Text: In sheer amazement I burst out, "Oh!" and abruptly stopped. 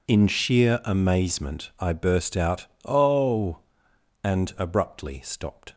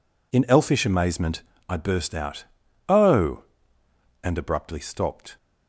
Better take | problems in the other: first | says "elfish" for "sheer"; at 0.4 s // pauses between "amazement" and "I"; slight; at 1.4 s; 0.26 s long

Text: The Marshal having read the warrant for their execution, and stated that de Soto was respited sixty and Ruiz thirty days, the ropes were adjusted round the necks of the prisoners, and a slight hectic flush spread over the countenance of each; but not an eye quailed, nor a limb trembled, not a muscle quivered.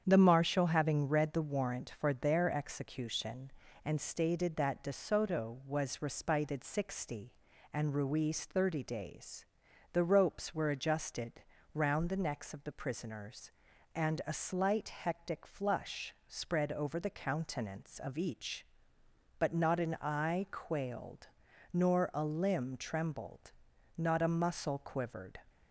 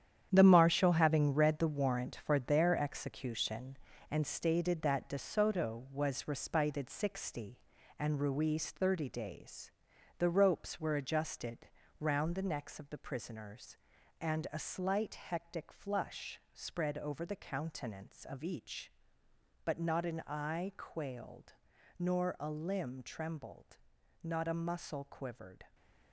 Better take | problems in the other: first | gets quieter; strong; throughout; 9 dB // starts louder than the rest; strong; until 1.3 s; 9.5 dB; strong in the first // pauses between "adjusted" and "round"; slight; at 11.6 s; 0.32 s long; slight in the first

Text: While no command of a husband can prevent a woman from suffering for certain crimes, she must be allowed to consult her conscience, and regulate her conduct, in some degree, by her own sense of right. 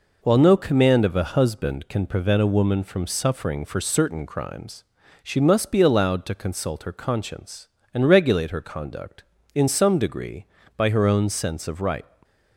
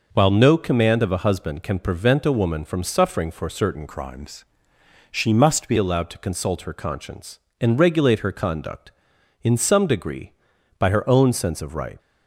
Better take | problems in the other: first | changes voice from "crimes" to "be"; from 3.8 to 5.7 s; 1.9 s long

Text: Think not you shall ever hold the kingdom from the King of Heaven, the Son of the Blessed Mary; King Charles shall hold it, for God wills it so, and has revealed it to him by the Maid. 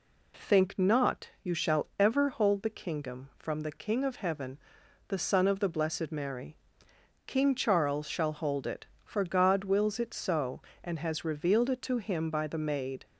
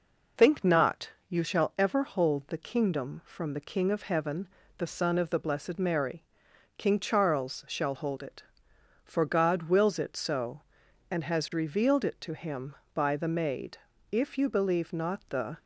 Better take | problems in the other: first | pauses between "not" and "you"; slight; at 1.0 s; 0.20 s long // goes on to say "If you believe not the"; from 14.1 s on; 1.4 s long

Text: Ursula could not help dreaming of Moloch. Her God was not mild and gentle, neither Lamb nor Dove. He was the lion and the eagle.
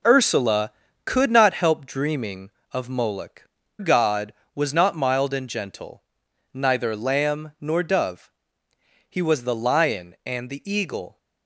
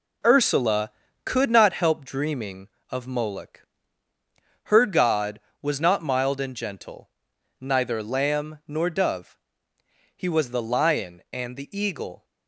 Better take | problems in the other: second | skips "Her"; at 3.6 s

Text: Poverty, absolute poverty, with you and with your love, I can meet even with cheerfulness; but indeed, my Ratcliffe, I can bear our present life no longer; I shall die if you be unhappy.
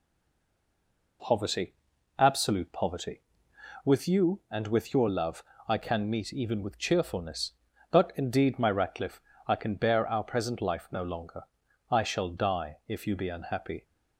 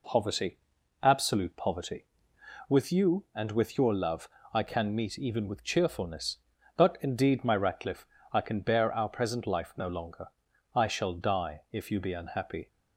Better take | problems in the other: second | stays silent before the first word; noticeable; until 1.2 s; 1.2 s long

